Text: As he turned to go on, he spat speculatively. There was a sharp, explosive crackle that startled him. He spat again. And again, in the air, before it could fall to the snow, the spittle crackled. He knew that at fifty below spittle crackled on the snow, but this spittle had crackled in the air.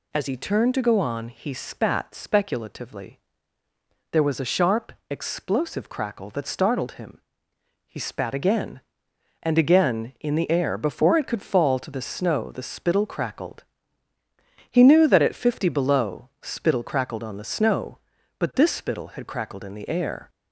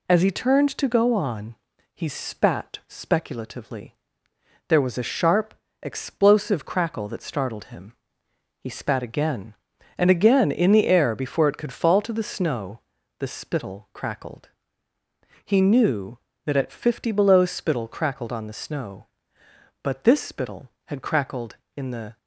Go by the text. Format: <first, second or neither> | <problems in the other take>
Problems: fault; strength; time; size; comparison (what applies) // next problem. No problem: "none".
first | stops before "air"; at 22.1 s